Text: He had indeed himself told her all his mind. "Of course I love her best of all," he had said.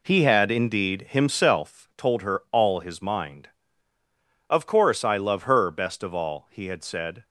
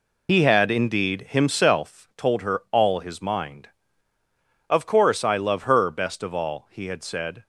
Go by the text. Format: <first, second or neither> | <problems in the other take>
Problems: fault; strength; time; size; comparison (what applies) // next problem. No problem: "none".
first | loses the start of "He"; at 0.2 s; 55 ms